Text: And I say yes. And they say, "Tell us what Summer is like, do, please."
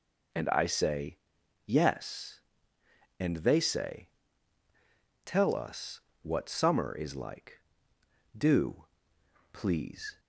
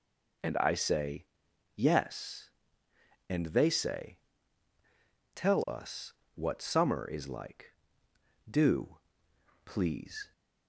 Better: neither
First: pauses between "say" and "yes"; noticeable; at 1.1 s; 0.48 s long // pauses between "us" and "what"; slight; at 6.0 s; 0.20 s long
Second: pauses between "say" and "yes"; noticeable; at 1.2 s; 0.50 s long // pauses between "us" and "what"; slight; at 6.1 s; 0.20 s long

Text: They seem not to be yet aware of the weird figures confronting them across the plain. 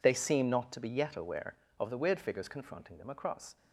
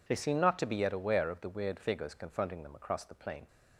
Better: second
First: stops before "the plain"; at 3.5 s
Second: none

